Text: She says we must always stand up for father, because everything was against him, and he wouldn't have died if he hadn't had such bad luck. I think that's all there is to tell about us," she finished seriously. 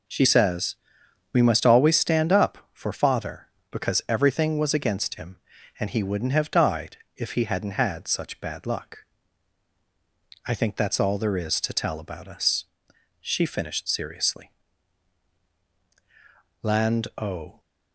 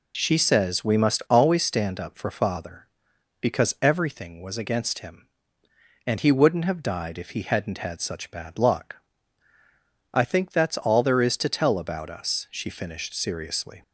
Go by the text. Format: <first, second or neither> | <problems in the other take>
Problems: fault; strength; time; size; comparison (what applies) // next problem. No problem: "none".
second | pauses between "says" and "we"; noticeable; at 0.7 s; 0.58 s long // pauses between "died" and "if"; slight; at 6.9 s; 0.18 s long // goes on to say "Land o"; noticeable; from 16.6 s on; 0.98 s long